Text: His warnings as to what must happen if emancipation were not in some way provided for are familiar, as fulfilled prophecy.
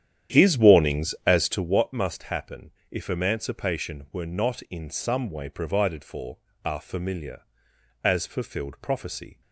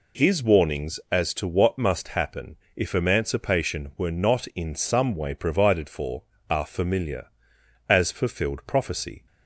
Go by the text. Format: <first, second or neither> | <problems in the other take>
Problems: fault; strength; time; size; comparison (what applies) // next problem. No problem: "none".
second | starts louder than the rest; strong; until 1.8 s; 9.5 dB // pauses between "happen" and "if"; slight; at 2.7 s; 0.18 s long; slight in the second